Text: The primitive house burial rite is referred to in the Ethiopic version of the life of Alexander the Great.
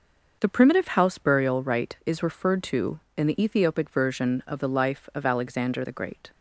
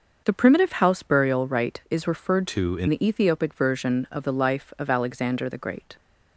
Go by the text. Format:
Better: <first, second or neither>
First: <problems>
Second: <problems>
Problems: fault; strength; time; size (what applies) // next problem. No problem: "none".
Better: first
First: starts louder than the rest; until 1.4 s; 6 dB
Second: starts louder than the rest; until 1.2 s; 6 dB // changes voice from "to" to "in"; from 2.4 to 2.8 s; 0.4 s long